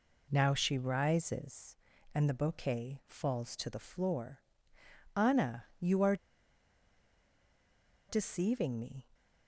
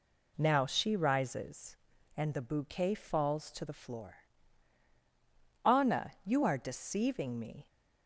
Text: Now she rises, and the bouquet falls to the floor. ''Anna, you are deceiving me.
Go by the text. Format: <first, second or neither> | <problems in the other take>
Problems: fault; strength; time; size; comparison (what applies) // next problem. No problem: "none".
second | pauses between "are" and "deceiving"; strong; at 6.1 s; 1.9 s long